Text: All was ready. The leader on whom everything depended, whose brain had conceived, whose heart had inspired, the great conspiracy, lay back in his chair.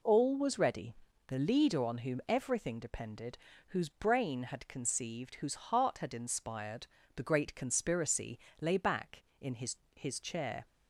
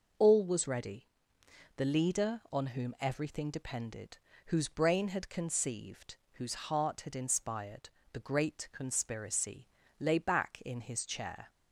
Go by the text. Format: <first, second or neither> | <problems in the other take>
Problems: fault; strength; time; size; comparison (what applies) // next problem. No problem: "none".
second | says "his" twice; at 9.9 s